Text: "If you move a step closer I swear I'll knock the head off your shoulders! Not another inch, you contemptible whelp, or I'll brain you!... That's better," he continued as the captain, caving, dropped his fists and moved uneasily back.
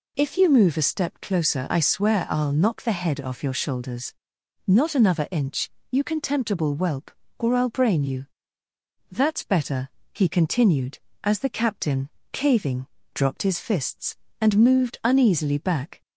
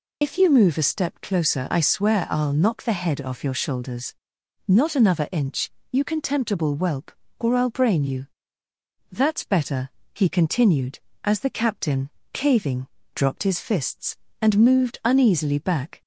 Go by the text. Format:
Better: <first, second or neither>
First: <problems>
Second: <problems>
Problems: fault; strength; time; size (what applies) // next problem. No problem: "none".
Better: first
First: none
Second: loses the start of "If"; at 0.2 s; 40 ms